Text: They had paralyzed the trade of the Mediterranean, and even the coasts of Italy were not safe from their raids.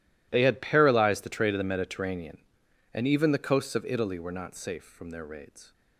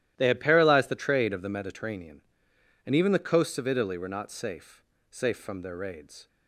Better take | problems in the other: first | starts louder than the rest; strong; until 1.1 s; 13.5 dB // says "safe" twice; at 5.0 s

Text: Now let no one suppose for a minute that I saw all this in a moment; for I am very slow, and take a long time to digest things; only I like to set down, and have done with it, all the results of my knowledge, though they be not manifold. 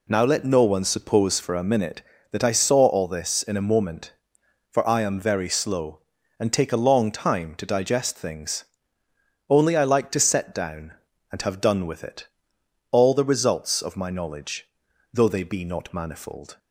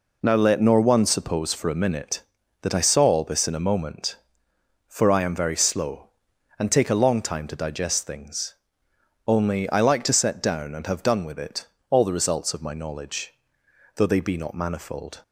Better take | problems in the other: first | says "nor" for "no"; at 0.6 s

